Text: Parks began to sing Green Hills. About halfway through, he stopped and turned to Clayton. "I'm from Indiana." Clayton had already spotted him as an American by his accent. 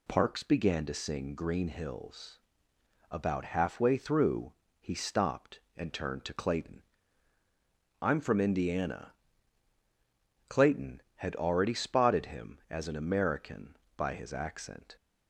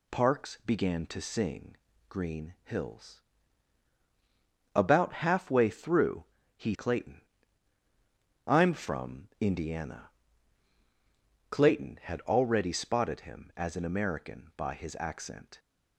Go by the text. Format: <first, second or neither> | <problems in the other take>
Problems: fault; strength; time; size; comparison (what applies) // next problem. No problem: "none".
first | pauses between "sing" and "Green"; slight; at 1.7 s; 0.32 s long // skips "stopped and turned to"; at 6.7 s